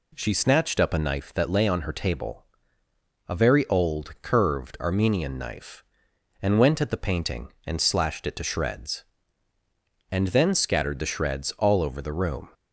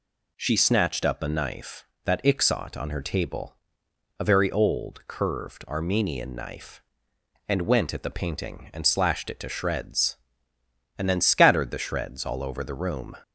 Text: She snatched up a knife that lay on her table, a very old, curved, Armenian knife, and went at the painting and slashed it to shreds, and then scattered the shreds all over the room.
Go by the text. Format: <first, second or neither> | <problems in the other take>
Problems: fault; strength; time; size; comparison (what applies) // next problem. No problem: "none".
first | says "ixot" for "lay"; at 2.2 s